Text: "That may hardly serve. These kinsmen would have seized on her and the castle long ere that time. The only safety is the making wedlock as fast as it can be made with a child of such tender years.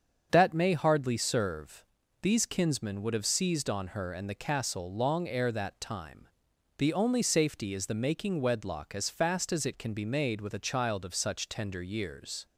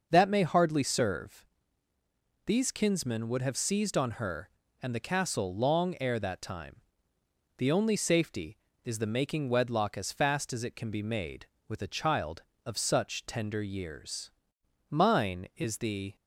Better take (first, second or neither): first